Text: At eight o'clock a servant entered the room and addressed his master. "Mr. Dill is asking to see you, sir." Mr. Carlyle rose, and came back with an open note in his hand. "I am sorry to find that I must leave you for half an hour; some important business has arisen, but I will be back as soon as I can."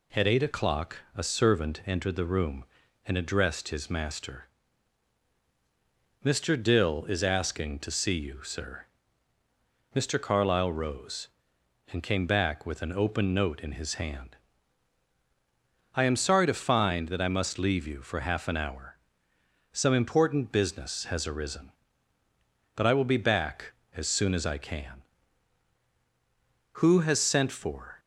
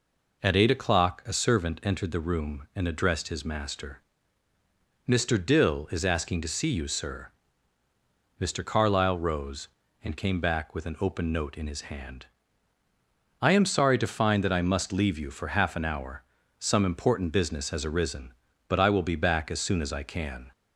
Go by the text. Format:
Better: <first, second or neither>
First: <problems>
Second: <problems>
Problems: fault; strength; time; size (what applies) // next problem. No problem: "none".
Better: second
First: pauses between "o'clock" and "a"; slight; at 0.9 s; 0.18 s long // goes on to say "Who has sent for"; noticeable; from 26.7 s on; 1.2 s long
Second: none